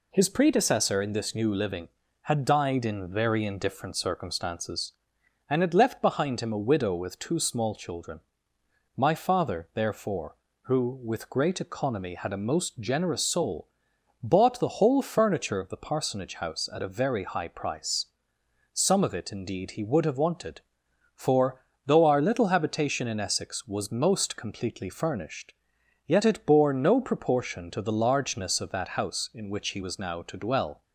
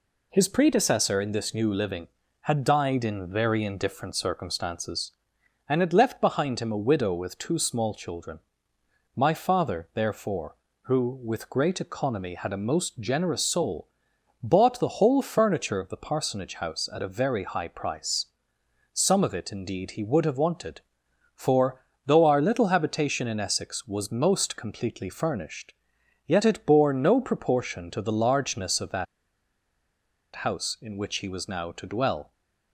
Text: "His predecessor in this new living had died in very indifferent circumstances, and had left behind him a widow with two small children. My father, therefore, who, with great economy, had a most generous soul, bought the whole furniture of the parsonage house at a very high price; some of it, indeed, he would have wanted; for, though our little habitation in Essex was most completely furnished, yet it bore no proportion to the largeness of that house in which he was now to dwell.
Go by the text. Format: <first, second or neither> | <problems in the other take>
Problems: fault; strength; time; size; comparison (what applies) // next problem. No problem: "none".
first | pauses between "that" and "house"; strong; at 29.0 s; 1.3 s long